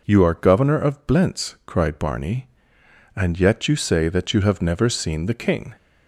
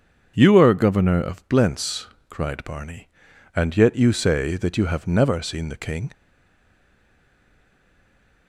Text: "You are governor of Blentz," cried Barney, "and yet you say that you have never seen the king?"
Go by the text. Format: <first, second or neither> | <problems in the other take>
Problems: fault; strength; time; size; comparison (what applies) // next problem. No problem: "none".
first | starts louder than the rest; until 1.3 s; 7 dB // stays silent after the last word; from 6.1 s on; 2.3 s long